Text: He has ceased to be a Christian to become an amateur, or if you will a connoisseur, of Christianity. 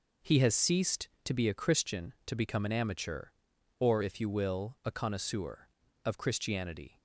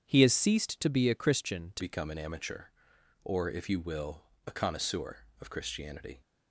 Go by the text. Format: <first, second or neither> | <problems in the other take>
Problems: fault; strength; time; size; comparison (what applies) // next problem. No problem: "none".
first | starts louder than the rest; strong; until 1.0 s; 7.5 dB // changes voice at "become"; from 1.8 s on; 4.4 s long // pauses between "will" and "a"; slight; at 4.2 s; 0.26 s long